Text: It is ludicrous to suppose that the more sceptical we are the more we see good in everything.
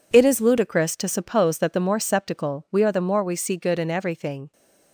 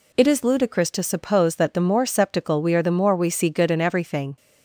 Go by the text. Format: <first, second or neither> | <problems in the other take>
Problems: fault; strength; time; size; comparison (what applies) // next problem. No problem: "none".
second | gets quieter; strong; throughout; 10.5 dB